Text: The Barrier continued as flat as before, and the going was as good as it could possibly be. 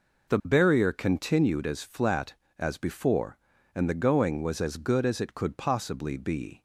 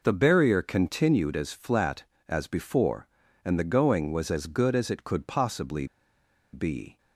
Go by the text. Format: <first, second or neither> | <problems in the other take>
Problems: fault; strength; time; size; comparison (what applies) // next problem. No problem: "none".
first | pauses between "possibly" and "be"; noticeable; at 5.8 s; 0.67 s long